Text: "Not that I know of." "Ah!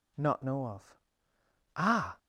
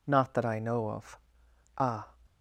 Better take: second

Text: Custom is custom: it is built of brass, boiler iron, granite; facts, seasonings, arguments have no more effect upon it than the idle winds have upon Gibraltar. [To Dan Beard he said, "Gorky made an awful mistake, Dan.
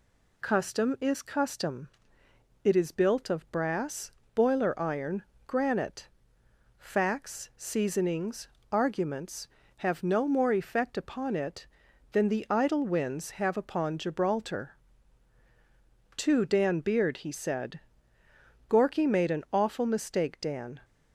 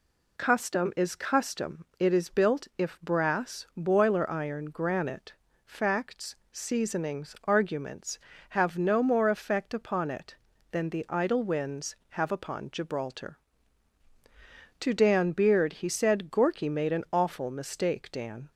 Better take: first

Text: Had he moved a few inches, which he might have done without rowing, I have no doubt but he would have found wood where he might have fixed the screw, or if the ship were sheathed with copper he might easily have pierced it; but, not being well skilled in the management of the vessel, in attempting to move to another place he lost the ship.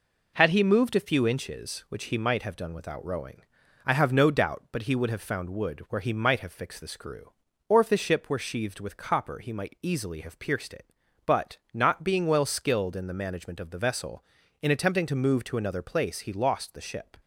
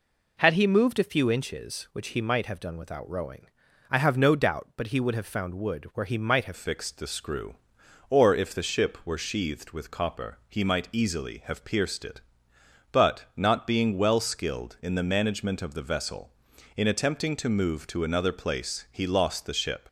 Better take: first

